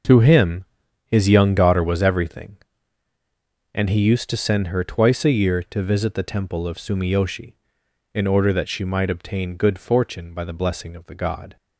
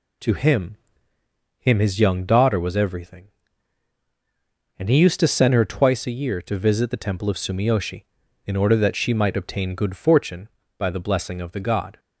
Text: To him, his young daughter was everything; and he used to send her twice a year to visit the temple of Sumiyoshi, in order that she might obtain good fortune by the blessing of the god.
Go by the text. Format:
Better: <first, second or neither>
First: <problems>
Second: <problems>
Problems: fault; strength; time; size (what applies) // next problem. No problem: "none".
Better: first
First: none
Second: says "him" twice; at 1.5 s